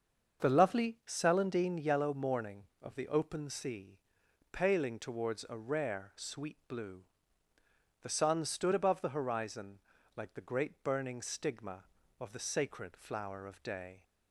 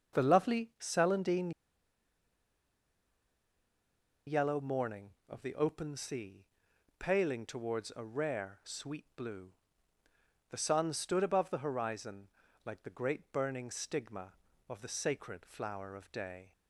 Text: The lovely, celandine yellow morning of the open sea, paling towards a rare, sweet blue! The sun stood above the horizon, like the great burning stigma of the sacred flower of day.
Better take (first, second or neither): first